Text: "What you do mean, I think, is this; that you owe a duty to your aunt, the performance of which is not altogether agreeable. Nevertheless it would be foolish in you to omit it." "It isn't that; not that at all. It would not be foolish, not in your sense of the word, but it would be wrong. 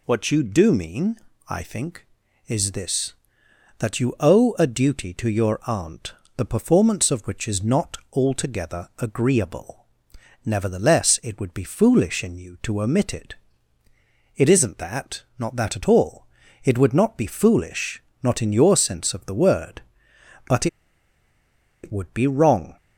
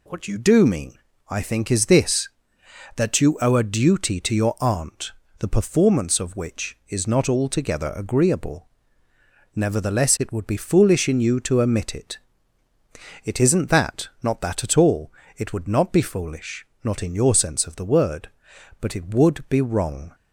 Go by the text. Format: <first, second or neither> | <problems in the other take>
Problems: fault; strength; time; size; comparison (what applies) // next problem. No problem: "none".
second | pauses between "not" and "altogether"; slight; at 7.9 s; 0.16 s long // pauses between "but" and "it"; at 20.6 s; 1.1 s long